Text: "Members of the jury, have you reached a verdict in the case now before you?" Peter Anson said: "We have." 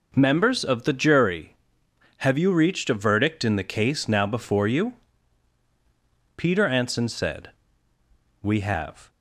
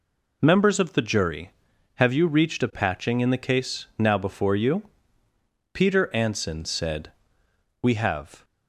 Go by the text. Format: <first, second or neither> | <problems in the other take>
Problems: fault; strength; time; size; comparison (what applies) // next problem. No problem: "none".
first | says "patching" for "verdict"; at 2.7 s